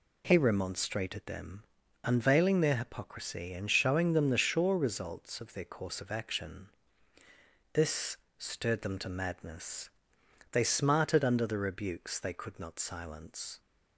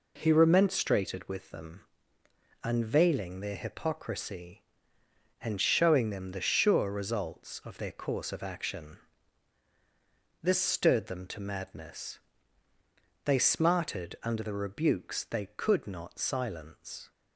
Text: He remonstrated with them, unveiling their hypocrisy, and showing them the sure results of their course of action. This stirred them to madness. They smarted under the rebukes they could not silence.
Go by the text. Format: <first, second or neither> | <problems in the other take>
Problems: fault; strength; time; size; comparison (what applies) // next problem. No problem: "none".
second | skips "with"; at 1.2 s // pauses between "This" and "stirred"; slight; at 8.1 s; 0.24 s long